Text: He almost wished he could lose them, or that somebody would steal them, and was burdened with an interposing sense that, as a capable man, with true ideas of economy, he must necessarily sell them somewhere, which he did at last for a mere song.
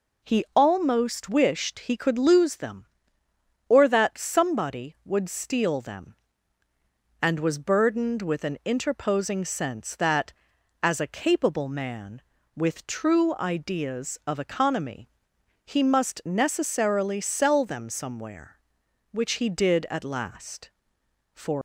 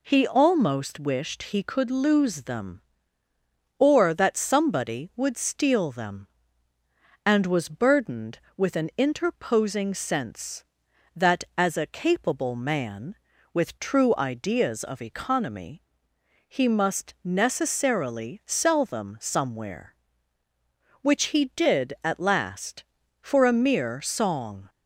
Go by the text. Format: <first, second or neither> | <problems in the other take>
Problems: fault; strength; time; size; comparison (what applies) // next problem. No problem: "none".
second | stops before "a mere song"; at 21.5 s